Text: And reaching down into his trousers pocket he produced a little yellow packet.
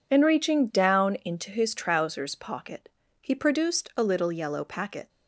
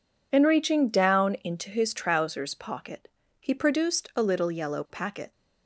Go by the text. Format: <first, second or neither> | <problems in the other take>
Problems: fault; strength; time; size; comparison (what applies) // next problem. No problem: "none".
neither | pauses between "pocket" and "he"; slight; the same in both